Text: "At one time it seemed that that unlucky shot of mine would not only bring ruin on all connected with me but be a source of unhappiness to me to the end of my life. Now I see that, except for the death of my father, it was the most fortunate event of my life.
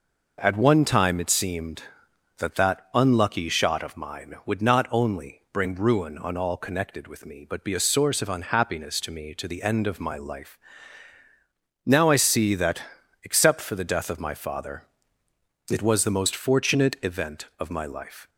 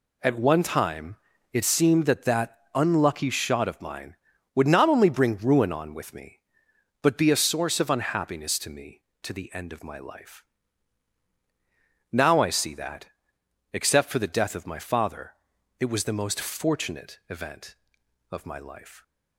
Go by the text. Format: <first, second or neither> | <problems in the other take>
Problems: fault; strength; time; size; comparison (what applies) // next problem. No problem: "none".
first | pauses between "time" and "it"; slight; at 1.1 s; 0.36 s long // pauses between "that" and "unlucky"; slight; at 2.5 s; 0.16 s long // skips "all connected"; at 5.9 s